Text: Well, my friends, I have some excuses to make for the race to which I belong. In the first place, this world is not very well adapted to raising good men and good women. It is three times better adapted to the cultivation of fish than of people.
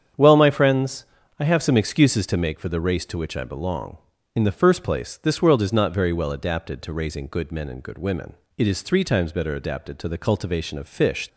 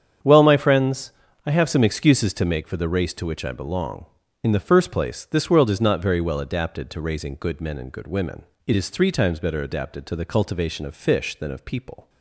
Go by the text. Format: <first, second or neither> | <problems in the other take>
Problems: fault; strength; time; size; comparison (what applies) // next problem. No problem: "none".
second | starts louder than the rest; strong; until 1.5 s; 8 dB; strong in the second // stops before "than of people"; at 11.2 s